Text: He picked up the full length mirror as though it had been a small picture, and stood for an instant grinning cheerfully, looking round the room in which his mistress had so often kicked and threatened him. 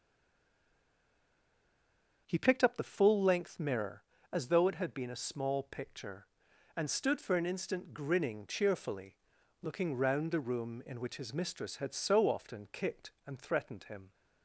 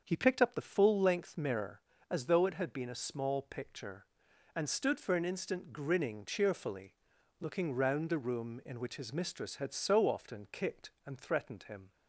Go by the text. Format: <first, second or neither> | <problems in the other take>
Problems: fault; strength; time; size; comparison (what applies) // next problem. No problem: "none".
second | stays silent before the first word; until 2.2 s; 2.2 s long // starts louder than the rest; until 3.2 s; 7 dB; also in the second